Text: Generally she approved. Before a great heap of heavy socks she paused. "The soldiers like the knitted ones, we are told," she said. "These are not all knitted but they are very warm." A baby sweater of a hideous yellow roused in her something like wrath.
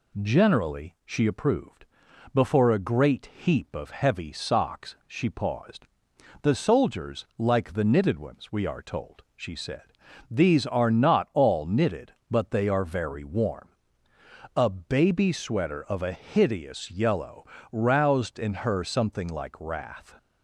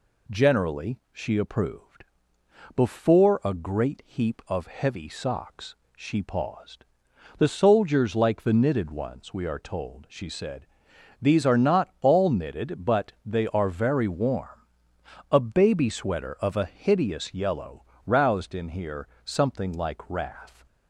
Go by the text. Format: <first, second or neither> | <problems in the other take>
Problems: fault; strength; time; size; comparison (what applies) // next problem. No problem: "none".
first | pauses between "socks" and "she"; slight; at 5.7 s; 0.20 s long // pauses between "yellow" and "roused"; slight; at 17.8 s; 0.20 s long; slight in the first // says "here" for "her"; at 18.6 s